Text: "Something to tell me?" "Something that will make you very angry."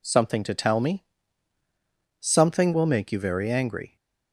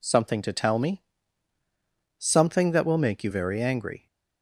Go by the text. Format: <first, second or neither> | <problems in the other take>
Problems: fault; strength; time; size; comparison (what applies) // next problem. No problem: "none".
second | skips "that"; at 2.7 s